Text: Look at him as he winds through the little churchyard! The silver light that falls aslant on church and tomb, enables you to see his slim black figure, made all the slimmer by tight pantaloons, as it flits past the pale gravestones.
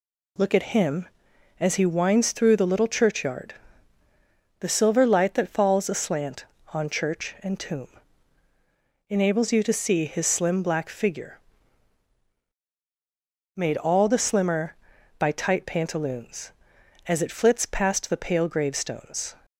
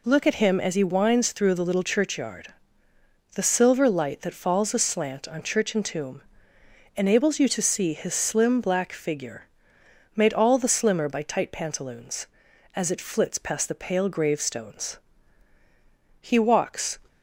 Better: first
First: none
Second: goes on to say "He walks"; noticeable; from 16.2 s on; 0.78 s long

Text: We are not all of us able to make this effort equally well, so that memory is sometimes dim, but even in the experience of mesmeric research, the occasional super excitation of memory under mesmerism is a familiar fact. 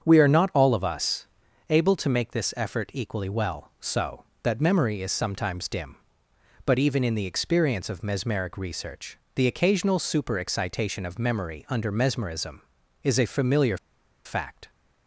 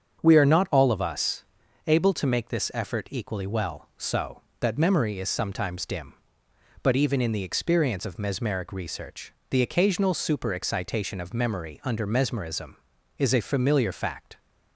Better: second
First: starts louder than the rest; strong; until 1.0 s; 7.5 dB // pauses between "us" and "able"; at 1.2 s; 0.42 s long // pauses between "familiar" and "fact"; noticeable; at 13.7 s; 0.48 s long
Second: starts louder than the rest; strong; until 1.2 s; 7 dB // pauses between "us" and "able"; at 1.4 s; 0.42 s long

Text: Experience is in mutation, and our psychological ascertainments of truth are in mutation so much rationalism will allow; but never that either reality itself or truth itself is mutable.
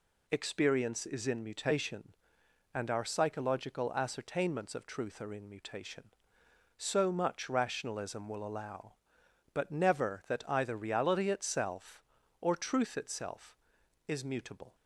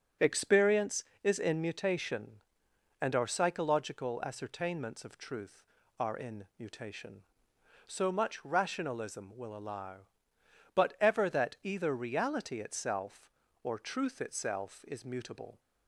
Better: first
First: none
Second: starts louder than the rest; until 1.4 s; 6.5 dB // says "ever" for "never"; at 10.9 s

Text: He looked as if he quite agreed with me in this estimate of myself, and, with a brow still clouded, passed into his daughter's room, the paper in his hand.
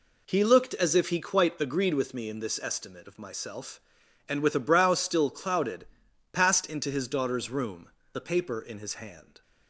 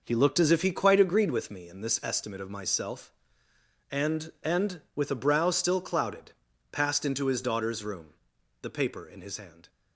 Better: first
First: none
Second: says "and" twice; at 4.4 s

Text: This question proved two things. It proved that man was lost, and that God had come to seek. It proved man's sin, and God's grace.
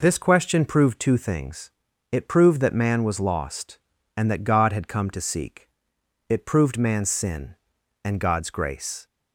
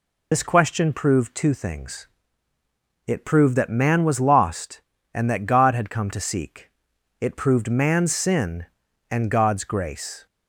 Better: first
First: none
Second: loses the start of "This"; at 0.3 s; 90 ms

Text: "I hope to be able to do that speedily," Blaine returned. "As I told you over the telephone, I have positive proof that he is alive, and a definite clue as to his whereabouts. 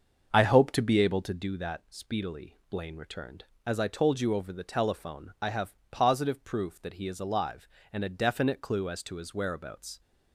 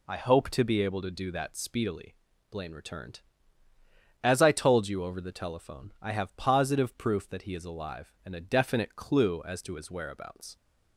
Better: second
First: starts louder than the rest; until 1.5 s; 6.5 dB // pauses between "have" and "positive"; slight; at 5.7 s; 0.16 s long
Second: none

